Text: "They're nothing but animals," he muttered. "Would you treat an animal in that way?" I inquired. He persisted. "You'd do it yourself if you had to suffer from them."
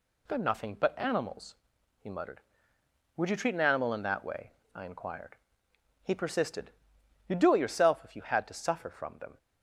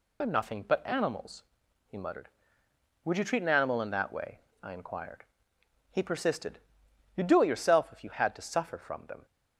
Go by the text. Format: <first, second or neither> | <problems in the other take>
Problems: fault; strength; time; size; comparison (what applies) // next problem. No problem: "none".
first | loses the start of "They're"; at 0.2 s; 45 ms